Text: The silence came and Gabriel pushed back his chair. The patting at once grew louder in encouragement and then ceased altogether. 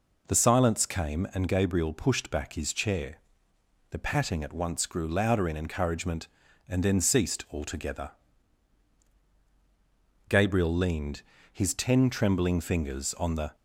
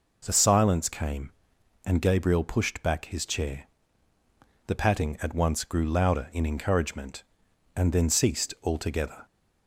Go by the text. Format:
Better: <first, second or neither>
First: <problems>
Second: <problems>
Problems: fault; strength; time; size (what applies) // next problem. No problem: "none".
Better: second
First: goes on to say "Gabriel leaned his ten trembling fingers on the"; strong; from 10.2 s on; 3.2 s long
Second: none